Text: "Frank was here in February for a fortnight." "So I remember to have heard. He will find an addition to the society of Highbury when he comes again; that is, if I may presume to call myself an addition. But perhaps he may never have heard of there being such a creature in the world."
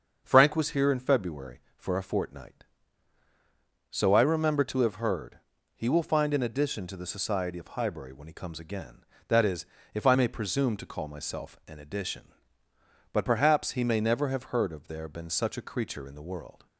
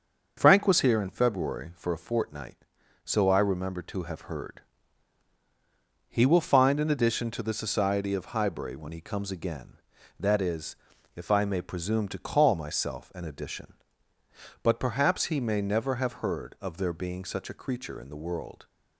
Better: second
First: starts louder than the rest; until 1.2 s; 7 dB // says "been" for "being"; at 15.0 s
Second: starts louder than the rest; until 1.3 s; 6.5 dB

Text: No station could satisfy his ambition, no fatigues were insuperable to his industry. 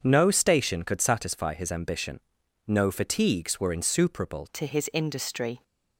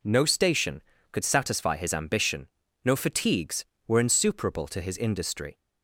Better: second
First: starts louder than the rest; until 1.0 s; 7 dB // changes voice at "to"; from 4.5 s on; 1.1 s long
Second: none

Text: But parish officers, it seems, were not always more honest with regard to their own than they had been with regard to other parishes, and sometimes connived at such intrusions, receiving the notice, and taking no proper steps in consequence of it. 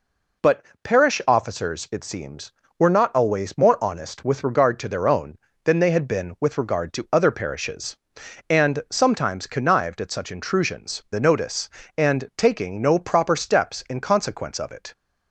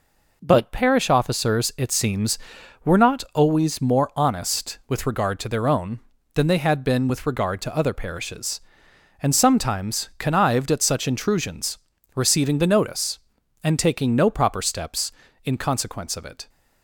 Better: second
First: pauses between "But" and "parish"; slight; at 0.6 s; 0.18 s long // skips "receiving"; at 11.0 s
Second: none

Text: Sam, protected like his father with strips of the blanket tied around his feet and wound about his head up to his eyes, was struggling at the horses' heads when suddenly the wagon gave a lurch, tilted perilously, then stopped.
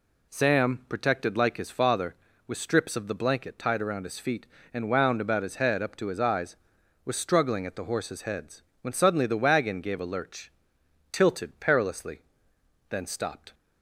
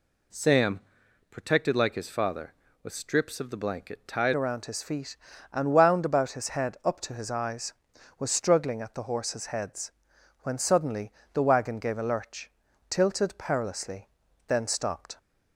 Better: first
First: pauses between "heads" and "when"; slight; at 8.6 s; 0.20 s long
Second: changes voice at "around"; from 4.3 s on; 10.8 s long // pauses between "heads" and "when"; noticeable; at 9.9 s; 0.52 s long // pauses between "suddenly" and "the"; slight; at 11.1 s; 0.22 s long

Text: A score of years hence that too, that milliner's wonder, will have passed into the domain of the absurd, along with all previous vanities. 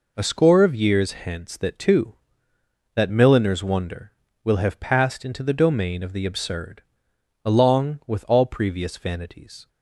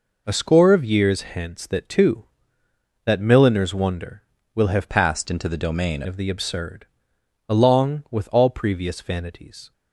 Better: first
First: none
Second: changes voice from "passed" to "domain"; from 4.8 to 6.0 s; 1.2 s long

